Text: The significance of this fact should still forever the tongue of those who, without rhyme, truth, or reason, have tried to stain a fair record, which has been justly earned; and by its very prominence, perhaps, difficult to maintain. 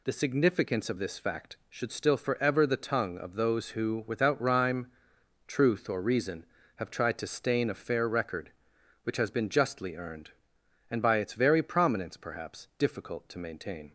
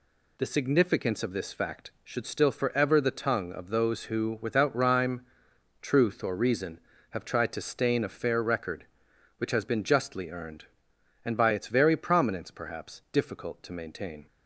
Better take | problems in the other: neither | none

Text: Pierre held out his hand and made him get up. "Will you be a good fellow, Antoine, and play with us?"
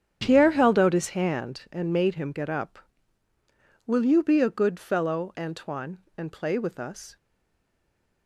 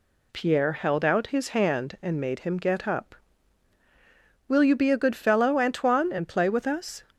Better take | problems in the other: second | starts louder than the rest; strong; until 1.2 s; 9.5 dB // stays silent after the last word; from 7.1 s on; 1.1 s long

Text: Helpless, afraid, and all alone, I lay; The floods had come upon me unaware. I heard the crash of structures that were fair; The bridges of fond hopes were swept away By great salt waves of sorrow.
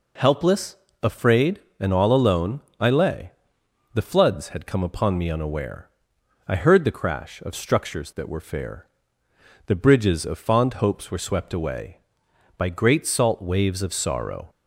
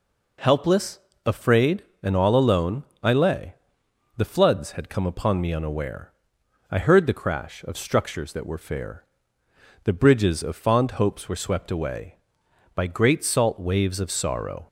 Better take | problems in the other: neither | none

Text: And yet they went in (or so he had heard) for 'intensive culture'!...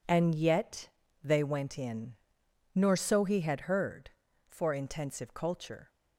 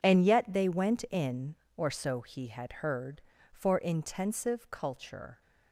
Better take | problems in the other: second | pauses between "yet" and "they"; slight; at 0.8 s; 0.34 s long // says "nor" for "or"; at 2.7 s

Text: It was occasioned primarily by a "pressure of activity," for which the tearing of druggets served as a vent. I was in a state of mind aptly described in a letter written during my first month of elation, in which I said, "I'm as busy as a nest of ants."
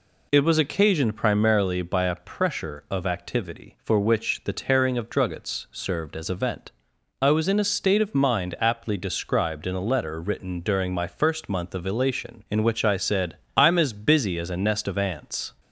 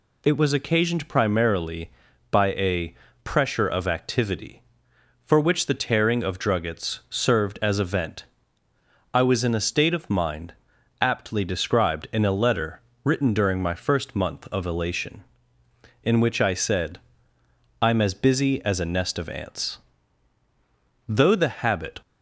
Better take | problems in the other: first | pauses between "a" and "pressure"; slight; at 2.9 s; 0.30 s long // pauses between "mind" and "aptly"; noticeable; at 10.5 s; 0.48 s long // pauses between "letter" and "written"; slight; at 12.8 s; 0.20 s long // goes on to say "Though the habit"; noticeable; from 21.0 s on; 0.92 s long

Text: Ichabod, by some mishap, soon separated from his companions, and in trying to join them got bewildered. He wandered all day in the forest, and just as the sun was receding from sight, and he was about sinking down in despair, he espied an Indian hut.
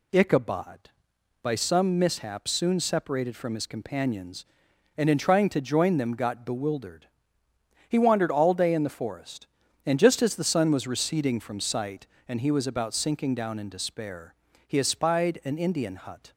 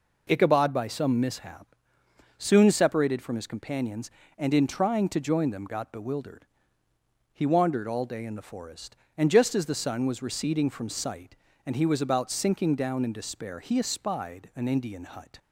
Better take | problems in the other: neither | none

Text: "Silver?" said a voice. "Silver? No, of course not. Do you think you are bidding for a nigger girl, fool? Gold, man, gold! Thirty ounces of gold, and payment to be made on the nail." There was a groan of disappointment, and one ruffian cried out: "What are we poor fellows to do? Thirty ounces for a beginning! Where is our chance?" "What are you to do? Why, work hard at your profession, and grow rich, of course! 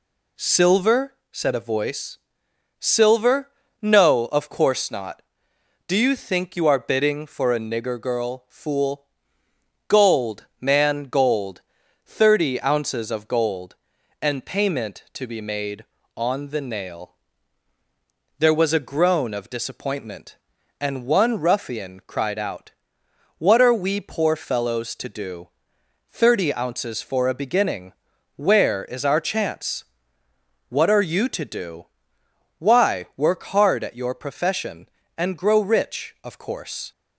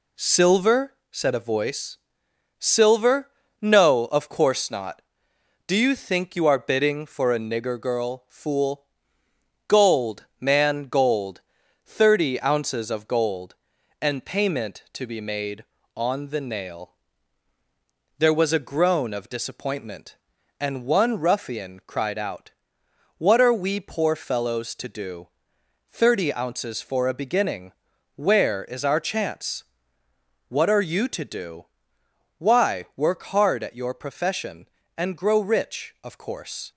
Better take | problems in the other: first | gets quieter; throughout; 4 dB

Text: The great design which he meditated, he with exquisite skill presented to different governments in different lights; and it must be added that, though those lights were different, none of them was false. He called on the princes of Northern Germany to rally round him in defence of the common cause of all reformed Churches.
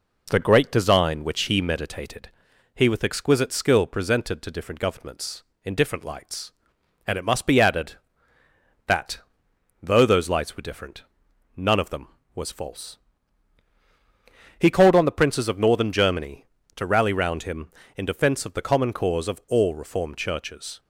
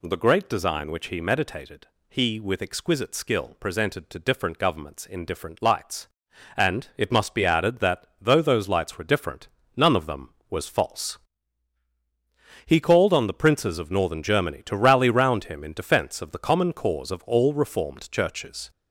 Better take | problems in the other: first | gets louder; noticeable; throughout; 4.5 dB

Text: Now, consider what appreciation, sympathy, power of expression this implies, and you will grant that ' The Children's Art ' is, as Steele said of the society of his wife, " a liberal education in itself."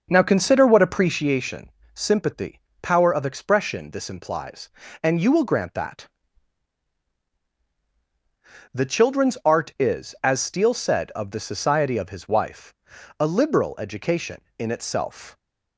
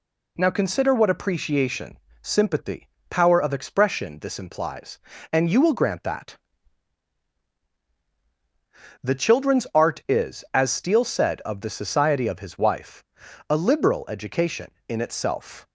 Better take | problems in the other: second | starts louder than the rest; strong; until 1.3 s; 7.5 dB

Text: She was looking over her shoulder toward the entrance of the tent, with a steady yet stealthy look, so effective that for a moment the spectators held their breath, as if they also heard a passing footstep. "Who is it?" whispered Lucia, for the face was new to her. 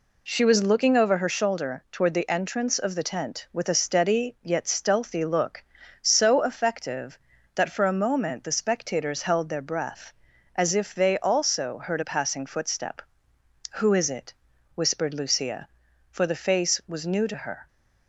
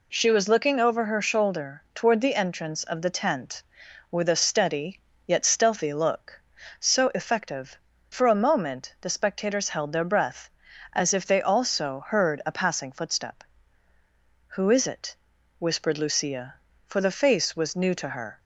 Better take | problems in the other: first | pauses between "steady" and "yet"; slight; at 4.9 s; 0.26 s long // skips "that"; at 7.9 s

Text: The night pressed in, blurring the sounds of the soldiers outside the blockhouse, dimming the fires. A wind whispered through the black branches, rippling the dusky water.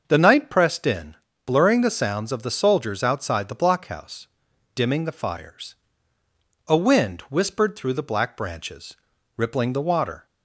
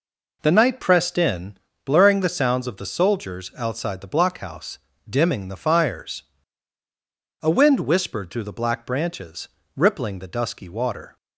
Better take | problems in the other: second | starts louder than the rest; until 1.0 s; 6.5 dB // skips "dusky"; at 9.8 s

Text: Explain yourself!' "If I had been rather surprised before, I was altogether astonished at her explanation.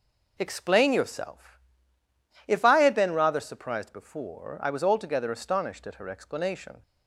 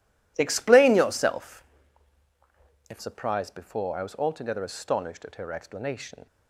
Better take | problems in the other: first | skips "I had been rather"; at 2.9 s

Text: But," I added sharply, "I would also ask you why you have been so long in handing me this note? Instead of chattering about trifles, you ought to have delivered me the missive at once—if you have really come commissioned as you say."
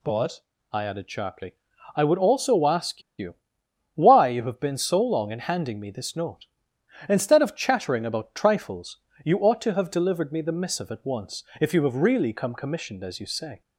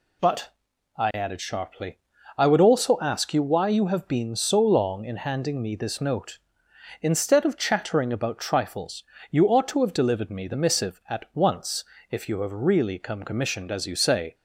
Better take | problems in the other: second | pauses between "ask" and "you"; slight; at 3.0 s; 0.17 s long // pauses between "you" and "why"; noticeable; at 3.3 s; 0.58 s long

